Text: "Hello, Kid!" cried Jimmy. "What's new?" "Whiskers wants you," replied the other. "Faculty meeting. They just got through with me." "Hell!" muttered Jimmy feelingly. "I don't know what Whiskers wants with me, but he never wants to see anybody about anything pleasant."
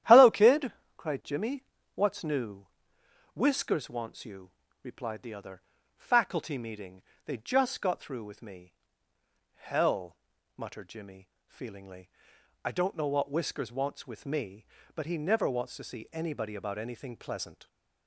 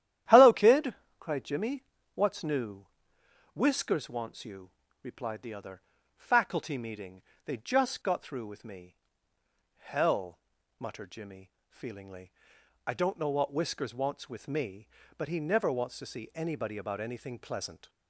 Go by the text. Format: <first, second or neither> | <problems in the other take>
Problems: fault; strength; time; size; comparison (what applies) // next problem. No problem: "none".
neither | starts louder than the rest; strong; the same in both // pauses between "Jimmy" and "feelingly"; slight; the same in both